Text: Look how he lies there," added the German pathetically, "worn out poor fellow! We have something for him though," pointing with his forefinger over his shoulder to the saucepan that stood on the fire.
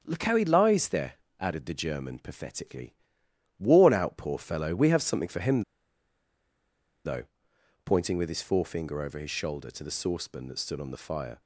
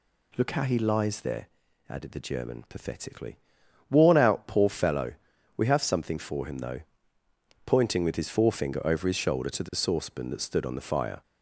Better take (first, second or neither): second